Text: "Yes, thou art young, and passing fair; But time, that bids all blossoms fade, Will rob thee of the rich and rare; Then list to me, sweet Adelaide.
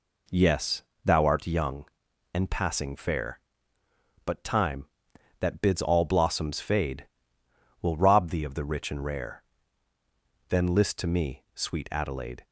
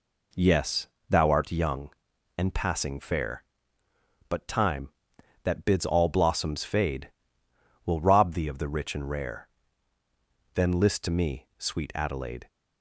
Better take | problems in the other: neither | none

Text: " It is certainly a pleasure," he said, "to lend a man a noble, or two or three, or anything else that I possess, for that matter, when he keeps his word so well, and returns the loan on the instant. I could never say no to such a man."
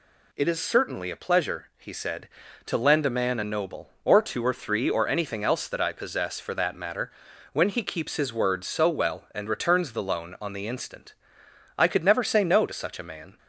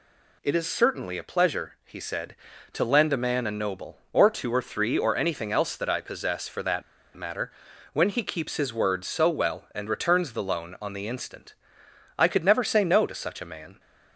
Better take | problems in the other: first | pauses between "that" and "matter"; slight; at 6.8 s; 0.32 s long

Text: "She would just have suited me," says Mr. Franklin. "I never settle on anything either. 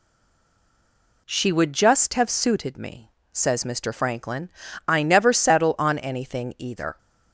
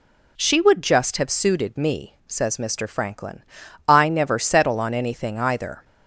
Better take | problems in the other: second | stays silent before the first word; noticeable; until 1.2 s; 1.2 s long

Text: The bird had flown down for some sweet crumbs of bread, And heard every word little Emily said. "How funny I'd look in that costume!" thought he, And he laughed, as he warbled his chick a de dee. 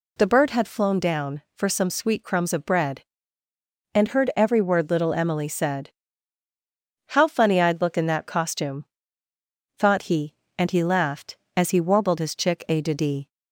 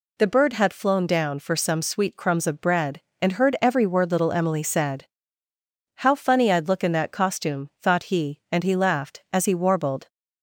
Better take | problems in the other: first | stops before "his chick a de dee"; at 10.0 s

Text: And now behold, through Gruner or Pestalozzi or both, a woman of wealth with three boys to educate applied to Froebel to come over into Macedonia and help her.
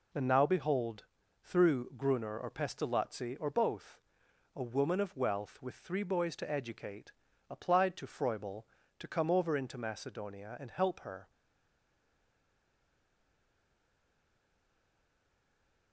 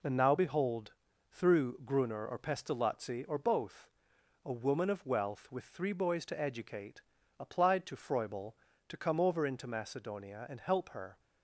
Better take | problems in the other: second | pauses between "educate" and "applied"; slight; at 7.1 s; 0.36 s long; slight in the second // stays silent after the last word; strong; from 11.2 s on; 4.7 s long

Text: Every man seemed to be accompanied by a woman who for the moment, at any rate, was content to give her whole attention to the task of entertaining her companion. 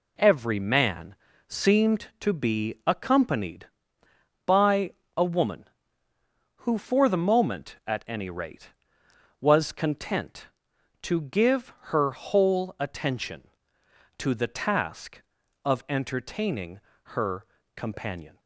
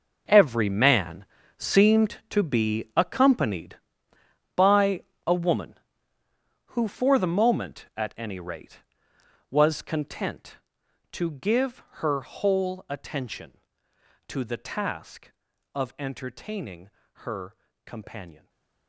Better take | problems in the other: first | gets quieter; strong; throughout; 14 dB // pauses between "man" and "seemed"; slight; at 1.2 s; 0.32 s long; slight in the first // pauses between "by" and "a"; slight; at 5.0 s; 0.24 s long; slight in the first // pauses between "entertaining" and "her"; slight; at 16.8 s; 0.34 s long; slight in the first // pauses between "her" and "companion"; slight; at 17.5 s; 0.30 s long; slight in the first // stays silent after the last word; slight; from 18.3 s on; 0.5 s long

